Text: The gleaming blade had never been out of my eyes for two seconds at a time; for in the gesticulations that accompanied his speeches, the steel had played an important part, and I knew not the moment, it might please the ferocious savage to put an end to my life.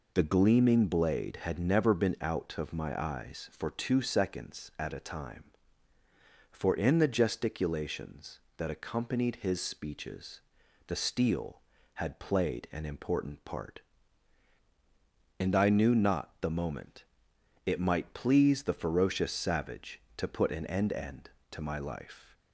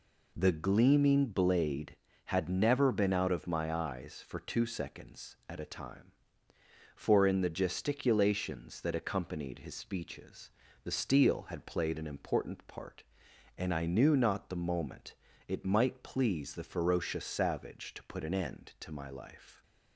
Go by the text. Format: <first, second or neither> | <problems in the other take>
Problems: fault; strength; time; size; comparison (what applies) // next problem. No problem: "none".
second | says "end" twice; at 20.9 s